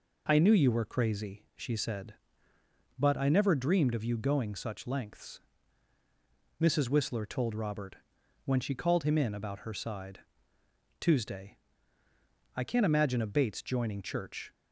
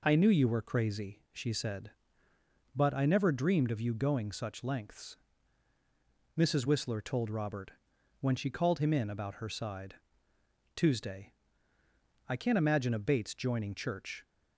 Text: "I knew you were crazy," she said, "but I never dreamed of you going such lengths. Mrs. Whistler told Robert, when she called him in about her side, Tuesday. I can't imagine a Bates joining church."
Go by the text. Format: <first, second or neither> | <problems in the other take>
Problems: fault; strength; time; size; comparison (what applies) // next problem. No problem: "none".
neither | none